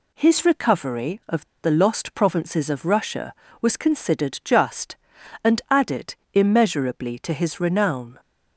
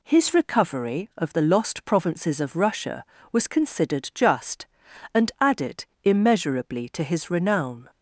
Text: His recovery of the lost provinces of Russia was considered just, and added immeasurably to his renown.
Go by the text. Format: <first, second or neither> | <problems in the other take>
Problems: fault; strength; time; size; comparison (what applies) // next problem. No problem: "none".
second | pauses between "of" and "the"; slight; at 1.4 s; 0.17 s long // pauses between "added" and "immeasurably"; slight; at 6.1 s; 0.18 s long; slight in the second